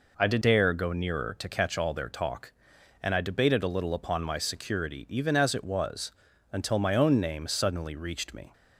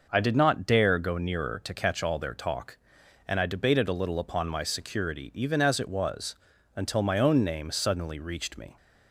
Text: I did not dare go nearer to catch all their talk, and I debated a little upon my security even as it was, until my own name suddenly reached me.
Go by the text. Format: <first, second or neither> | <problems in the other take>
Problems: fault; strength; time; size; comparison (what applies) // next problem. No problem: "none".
second | skips "not"; at 0.4 s